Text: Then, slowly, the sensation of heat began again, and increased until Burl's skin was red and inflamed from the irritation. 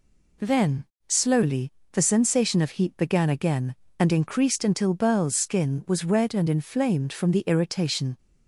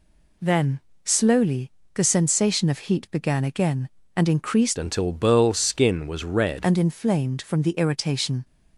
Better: first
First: none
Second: changes voice from "until" to "red"; from 4.7 to 6.6 s; 1.9 s long

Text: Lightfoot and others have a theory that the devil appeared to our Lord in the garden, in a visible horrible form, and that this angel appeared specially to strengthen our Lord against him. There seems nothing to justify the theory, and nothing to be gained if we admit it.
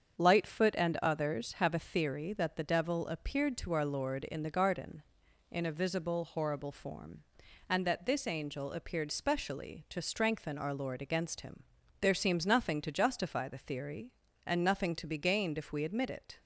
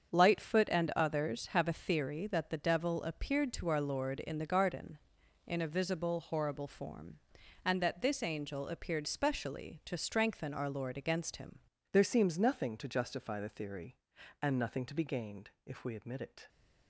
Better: first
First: starts louder than the rest; strong; until 1.2 s; 7.5 dB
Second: starts louder than the rest; strong; until 1.1 s; 7.5 dB // changes voice at "There"; from 11.9 s on; 4.5 s long // pauses between "gained" and "if"; slight; at 15.4 s; 0.16 s long

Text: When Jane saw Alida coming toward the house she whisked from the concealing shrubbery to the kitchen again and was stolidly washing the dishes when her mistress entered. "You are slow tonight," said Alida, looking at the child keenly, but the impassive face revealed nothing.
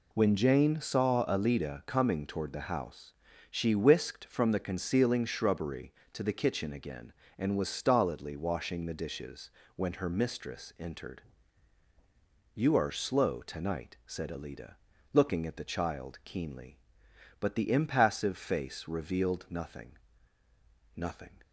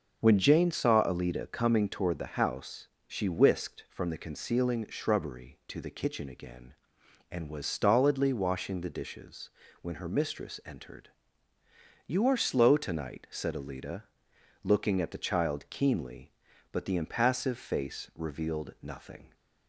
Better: second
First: pauses between "house" and "she"; slight; at 3.1 s; 0.36 s long // pauses between "dishes" and "when"; slight; at 9.5 s; 0.24 s long // says "nothing" twice; at 20.9 s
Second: pauses between "house" and "she"; slight; at 2.8 s; 0.20 s long // pauses between "dishes" and "when"; slight; at 9.4 s; 0.32 s long

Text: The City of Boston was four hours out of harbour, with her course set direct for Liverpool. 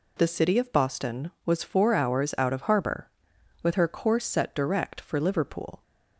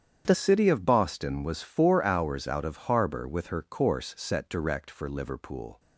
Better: first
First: none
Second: starts louder than the rest; strong; until 1.2 s; 8.5 dB // changes voice at "City"; from 0.3 s on; 5.4 s long

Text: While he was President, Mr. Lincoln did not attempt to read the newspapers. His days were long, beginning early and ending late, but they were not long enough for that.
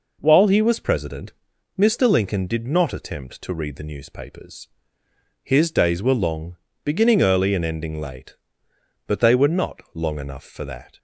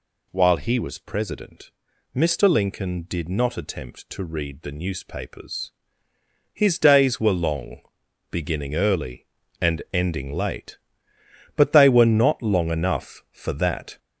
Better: first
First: none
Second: gets louder; noticeable; throughout; 5.5 dB

